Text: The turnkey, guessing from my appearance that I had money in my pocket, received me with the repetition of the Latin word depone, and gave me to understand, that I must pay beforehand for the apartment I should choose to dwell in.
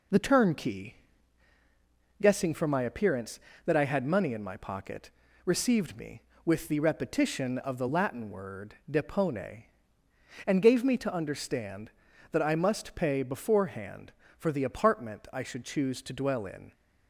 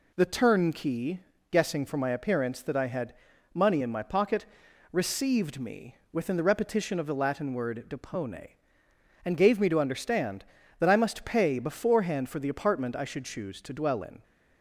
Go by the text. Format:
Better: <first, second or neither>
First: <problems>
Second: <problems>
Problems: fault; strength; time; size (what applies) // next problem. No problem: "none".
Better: first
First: none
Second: pauses between "had" and "money"; at 3.1 s; 0.40 s long // says "within" for "with"; at 6.1 s